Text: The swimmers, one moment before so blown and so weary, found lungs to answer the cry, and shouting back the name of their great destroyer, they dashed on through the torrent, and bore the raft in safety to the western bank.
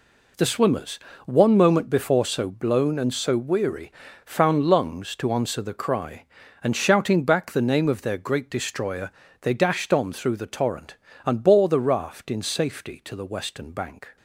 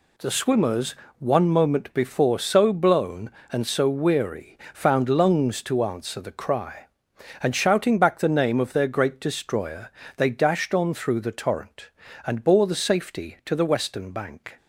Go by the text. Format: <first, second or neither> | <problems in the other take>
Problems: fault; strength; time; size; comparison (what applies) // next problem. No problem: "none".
first | skips "raft in"; at 12.7 s